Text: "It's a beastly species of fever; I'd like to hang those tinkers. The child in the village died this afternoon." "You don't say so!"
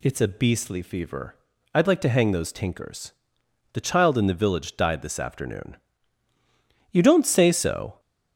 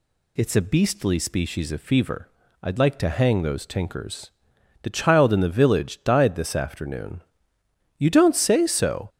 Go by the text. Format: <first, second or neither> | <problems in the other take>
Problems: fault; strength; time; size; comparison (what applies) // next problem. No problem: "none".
second | skips "species of"; at 0.8 s